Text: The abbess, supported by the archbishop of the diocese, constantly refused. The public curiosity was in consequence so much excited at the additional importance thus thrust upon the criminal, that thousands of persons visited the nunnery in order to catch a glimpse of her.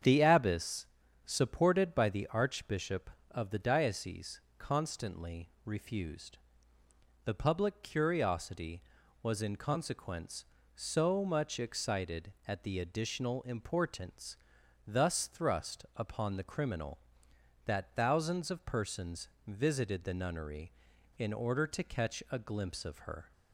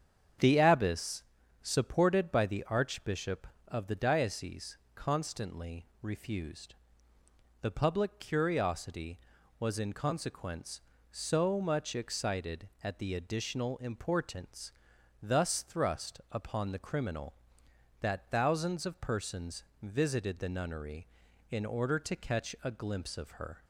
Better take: neither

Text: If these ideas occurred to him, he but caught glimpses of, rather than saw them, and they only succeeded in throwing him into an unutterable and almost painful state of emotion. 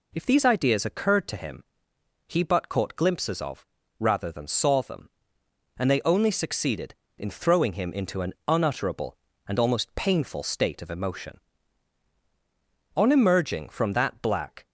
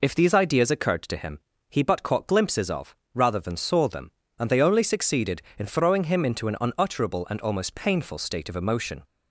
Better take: second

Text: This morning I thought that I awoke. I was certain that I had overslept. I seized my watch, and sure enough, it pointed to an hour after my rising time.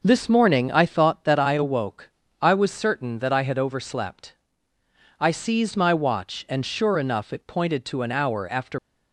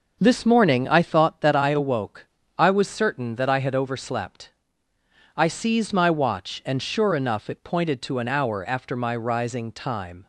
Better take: second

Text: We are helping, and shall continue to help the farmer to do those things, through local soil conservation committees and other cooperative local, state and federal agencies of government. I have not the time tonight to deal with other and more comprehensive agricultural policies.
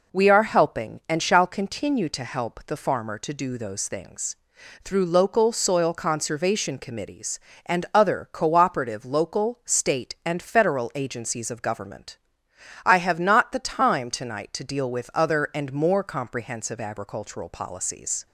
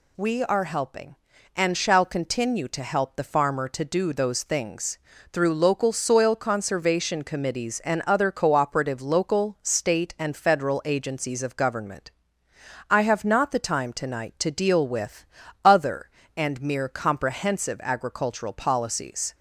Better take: first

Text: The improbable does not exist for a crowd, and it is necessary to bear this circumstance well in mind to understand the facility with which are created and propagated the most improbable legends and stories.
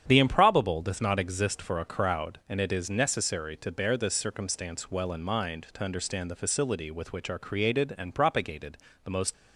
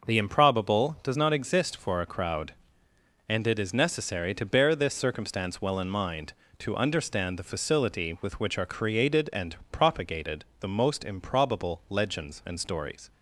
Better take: second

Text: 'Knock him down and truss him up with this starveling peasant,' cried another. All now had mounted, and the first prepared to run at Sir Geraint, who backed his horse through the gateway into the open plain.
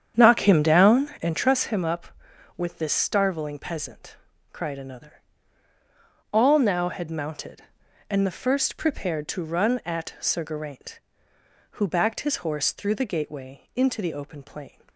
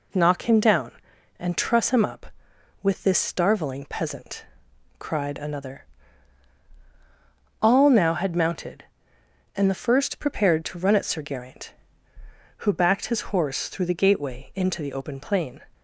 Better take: second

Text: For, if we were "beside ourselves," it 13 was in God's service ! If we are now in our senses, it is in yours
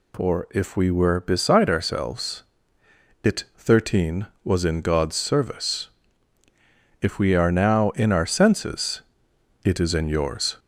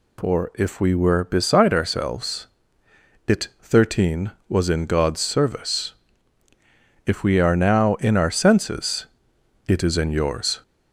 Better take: neither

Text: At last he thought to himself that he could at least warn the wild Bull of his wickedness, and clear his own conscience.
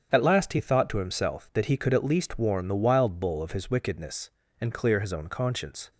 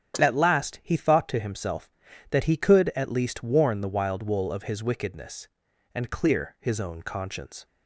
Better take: first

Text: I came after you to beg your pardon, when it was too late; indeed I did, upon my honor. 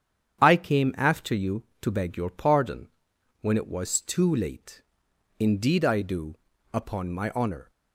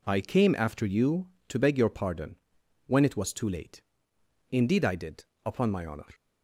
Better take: second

